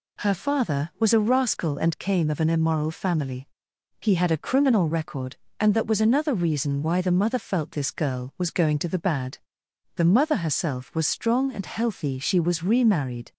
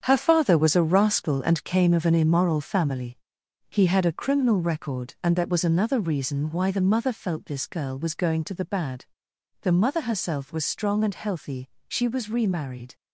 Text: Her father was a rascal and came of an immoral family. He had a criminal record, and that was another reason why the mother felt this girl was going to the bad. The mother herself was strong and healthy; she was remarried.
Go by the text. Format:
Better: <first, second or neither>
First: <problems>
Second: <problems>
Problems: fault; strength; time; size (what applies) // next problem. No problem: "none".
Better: first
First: none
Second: gets quieter; strong; throughout; 8.5 dB